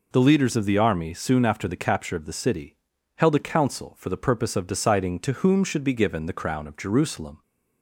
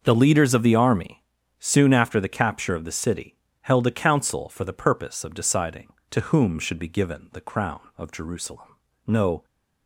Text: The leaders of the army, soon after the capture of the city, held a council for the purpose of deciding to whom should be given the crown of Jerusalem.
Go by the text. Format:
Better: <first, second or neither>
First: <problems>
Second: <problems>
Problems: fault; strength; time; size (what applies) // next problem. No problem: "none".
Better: first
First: none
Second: goes on to say "No"; slight; from 9.0 s on; 0.38 s long